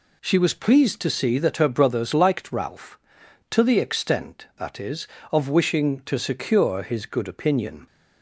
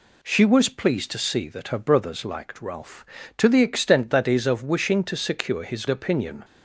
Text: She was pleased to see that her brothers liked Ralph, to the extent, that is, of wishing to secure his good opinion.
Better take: first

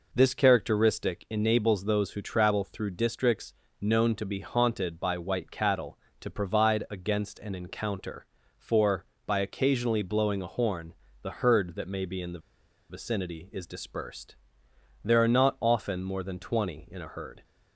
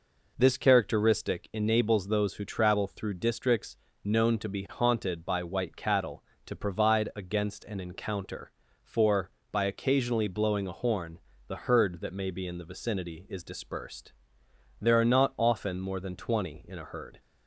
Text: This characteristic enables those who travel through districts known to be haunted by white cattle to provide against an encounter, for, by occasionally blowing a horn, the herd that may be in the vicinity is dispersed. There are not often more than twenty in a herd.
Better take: second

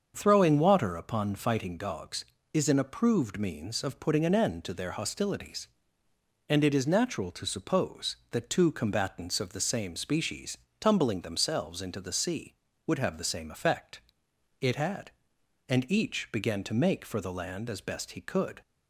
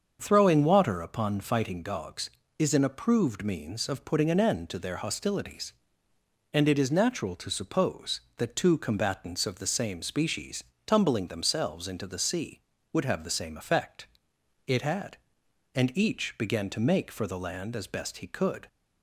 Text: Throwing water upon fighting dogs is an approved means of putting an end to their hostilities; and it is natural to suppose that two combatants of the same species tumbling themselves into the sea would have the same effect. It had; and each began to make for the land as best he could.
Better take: neither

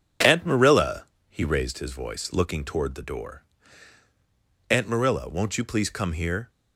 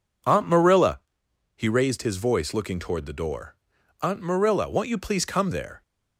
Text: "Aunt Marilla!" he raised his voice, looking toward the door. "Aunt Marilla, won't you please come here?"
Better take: first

